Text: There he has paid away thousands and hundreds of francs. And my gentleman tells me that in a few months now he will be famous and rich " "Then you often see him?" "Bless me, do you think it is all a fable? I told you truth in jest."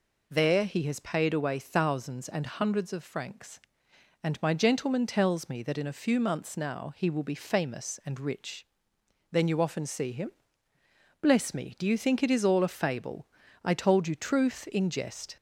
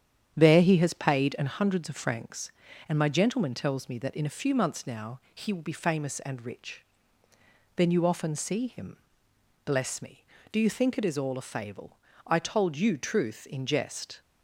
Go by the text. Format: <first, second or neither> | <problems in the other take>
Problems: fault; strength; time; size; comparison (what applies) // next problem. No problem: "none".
first | starts louder than the rest; strong; until 1.3 s; 9.5 dB // skips "away thousands"; at 1.3 s